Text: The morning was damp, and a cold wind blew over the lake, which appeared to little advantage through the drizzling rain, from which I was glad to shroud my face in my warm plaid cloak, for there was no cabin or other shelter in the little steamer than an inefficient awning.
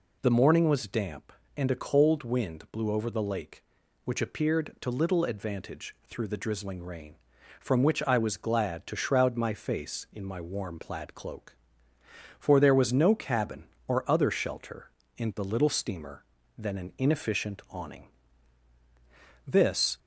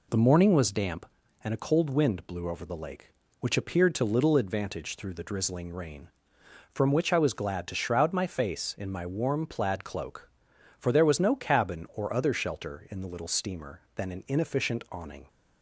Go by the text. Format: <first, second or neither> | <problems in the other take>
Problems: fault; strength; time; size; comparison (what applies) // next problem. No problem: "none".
second | goes on to say "This"; from 19.4 s on; 0.54 s long